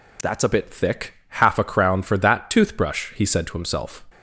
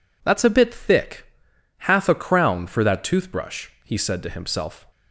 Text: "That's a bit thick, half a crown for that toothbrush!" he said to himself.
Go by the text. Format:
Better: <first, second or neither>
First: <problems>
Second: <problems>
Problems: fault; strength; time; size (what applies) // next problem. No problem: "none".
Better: neither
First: none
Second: none